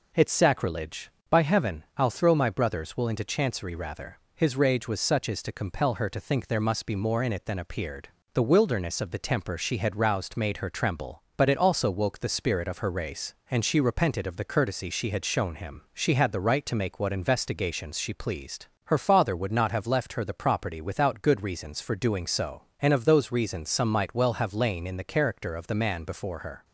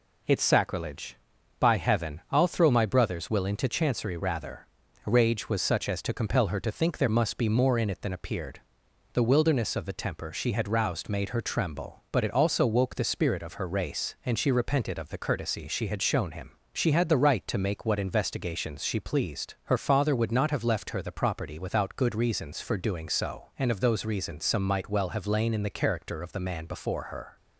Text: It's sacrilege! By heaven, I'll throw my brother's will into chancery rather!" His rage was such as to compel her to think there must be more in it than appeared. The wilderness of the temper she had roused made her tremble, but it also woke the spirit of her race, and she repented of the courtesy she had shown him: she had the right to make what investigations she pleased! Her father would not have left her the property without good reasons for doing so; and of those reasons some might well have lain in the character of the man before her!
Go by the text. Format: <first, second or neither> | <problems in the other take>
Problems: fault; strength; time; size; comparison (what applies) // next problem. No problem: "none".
first | skips "His"; at 4.8 s